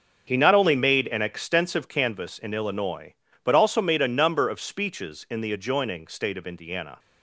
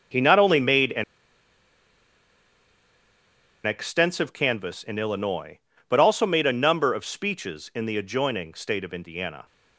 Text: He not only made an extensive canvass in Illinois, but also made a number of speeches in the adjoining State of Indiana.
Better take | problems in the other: first | starts louder than the rest; until 3.7 s; 7 dB; also in the first // pauses between "an" and "extensive"; strong; at 1.0 s; 2.6 s long

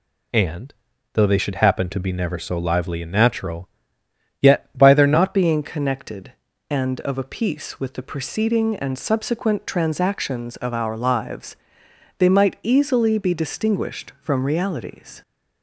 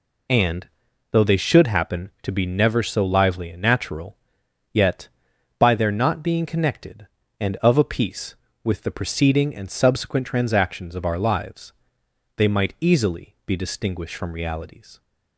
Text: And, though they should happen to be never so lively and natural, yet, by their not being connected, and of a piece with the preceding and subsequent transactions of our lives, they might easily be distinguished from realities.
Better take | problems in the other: second | changes voice at "being"; from 5.3 s on; 9.9 s long

